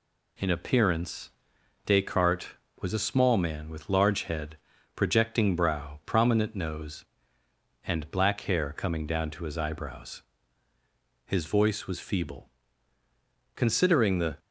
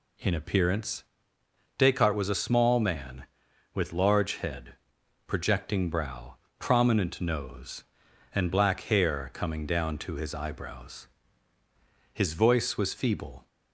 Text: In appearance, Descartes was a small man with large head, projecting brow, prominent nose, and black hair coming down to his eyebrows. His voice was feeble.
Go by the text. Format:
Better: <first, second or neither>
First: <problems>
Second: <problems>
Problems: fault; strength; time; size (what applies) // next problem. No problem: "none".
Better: second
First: goes on to say "Considering the"; noticeable; from 13.5 s on; 0.82 s long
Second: none